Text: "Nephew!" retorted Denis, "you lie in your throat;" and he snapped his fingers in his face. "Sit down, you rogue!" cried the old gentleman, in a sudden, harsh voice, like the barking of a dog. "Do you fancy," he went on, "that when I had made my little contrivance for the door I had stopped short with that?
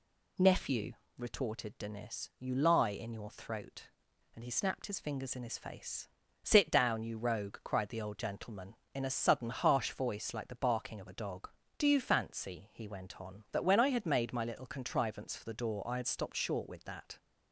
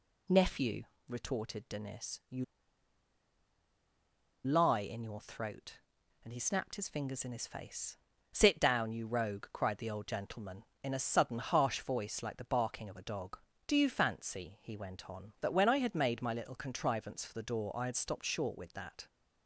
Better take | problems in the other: first | pauses between "you" and "lie"; strong; at 2.4 s; 2.0 s long

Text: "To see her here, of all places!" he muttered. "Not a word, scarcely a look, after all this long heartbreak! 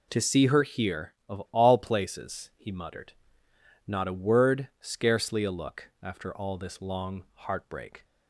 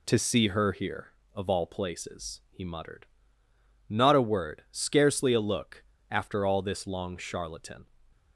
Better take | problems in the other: first | says "charlatan" for "heartbreak"; at 7.1 s

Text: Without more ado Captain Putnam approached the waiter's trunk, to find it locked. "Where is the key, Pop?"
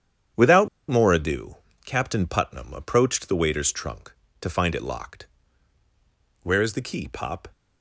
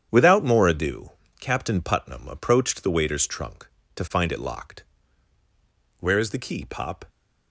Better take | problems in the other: second | starts louder than the rest; strong; until 1.5 s; 8.5 dB; strong in the second // pauses between "Without" and "more"; slight; at 0.6 s; 0.20 s long // pauses between "ado" and "Captain"; slight; at 1.5 s; 0.28 s long; slight in the second

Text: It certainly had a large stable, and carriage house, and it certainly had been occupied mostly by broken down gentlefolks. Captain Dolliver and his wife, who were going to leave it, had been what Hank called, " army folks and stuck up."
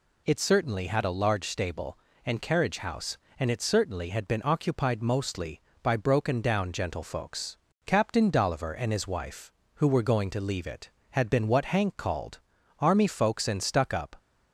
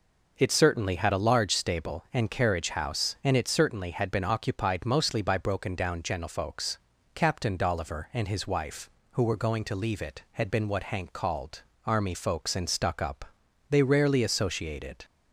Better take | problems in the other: first | goes on to say "They rarely associated"; from 13.6 s on; 1.3 s long

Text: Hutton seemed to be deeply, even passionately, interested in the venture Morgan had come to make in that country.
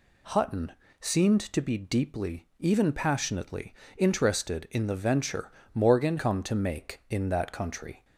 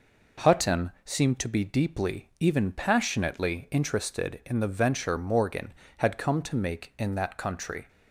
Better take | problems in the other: second | pauses between "Hutton" and "seemed"; slight; at 0.7 s; 0.28 s long // pauses between "venture" and "Morgan"; slight; at 5.5 s; 0.20 s long // skips "had"; at 6.1 s

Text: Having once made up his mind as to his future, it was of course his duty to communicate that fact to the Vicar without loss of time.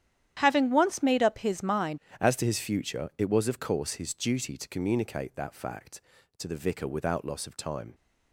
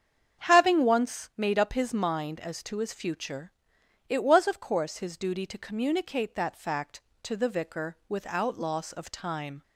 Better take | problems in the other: second | starts louder than the rest; strong; until 1.3 s; 10.5 dB; strong in the second // changes voice at "as"; from 2.1 s on; 5.8 s long

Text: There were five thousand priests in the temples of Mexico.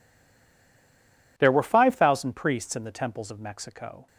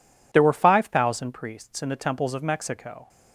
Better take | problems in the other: second | stays silent before the first word; noticeable; until 1.3 s; 1.3 s long

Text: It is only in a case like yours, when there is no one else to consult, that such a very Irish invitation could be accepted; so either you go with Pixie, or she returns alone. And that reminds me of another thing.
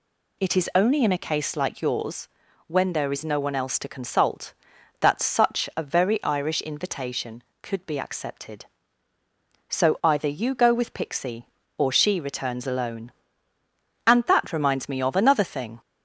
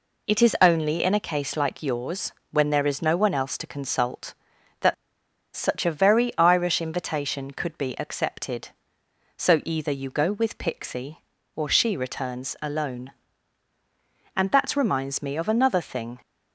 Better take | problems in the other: first | pauses between "that" and "such"; noticeable; at 4.9 s; 0.61 s long

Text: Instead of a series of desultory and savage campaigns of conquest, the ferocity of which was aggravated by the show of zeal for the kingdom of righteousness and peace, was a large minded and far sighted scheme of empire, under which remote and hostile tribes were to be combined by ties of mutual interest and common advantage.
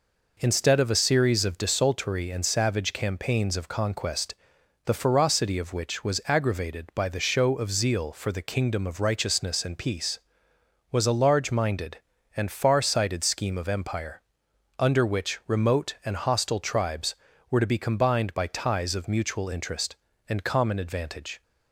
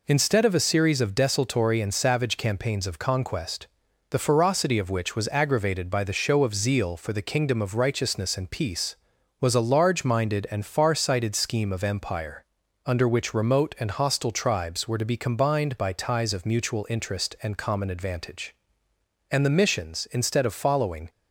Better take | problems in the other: first | goes on to say "And the missions instead of following"; strong; from 19.3 s on; 1.7 s long

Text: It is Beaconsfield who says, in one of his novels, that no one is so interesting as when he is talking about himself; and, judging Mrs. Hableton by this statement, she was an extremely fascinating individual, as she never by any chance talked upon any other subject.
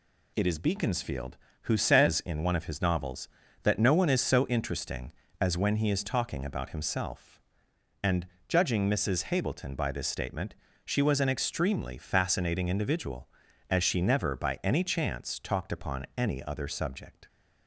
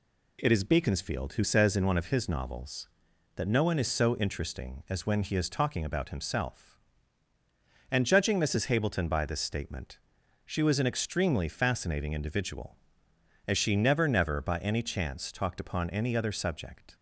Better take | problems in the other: first | says "never" twice; at 14.0 s

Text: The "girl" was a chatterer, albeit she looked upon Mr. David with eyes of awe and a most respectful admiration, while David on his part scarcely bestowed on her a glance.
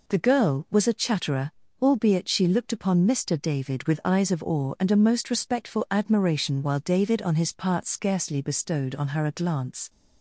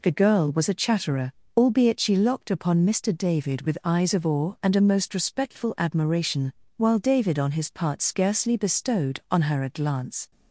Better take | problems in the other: first | says "locked" for "looked"; at 2.1 s

